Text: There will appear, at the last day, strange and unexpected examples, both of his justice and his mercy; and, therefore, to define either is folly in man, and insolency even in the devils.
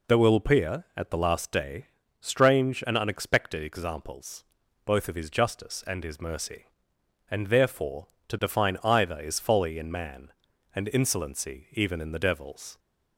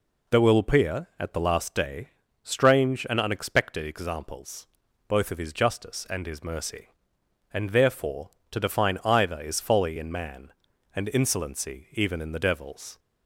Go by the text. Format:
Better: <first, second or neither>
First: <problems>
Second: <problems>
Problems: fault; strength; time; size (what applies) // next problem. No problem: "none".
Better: neither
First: none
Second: none